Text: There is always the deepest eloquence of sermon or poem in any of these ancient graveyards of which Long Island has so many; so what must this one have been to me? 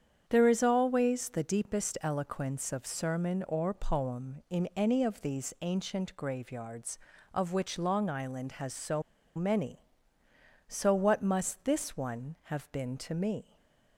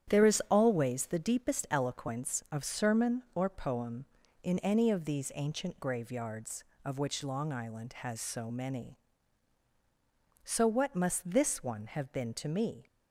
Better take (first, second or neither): second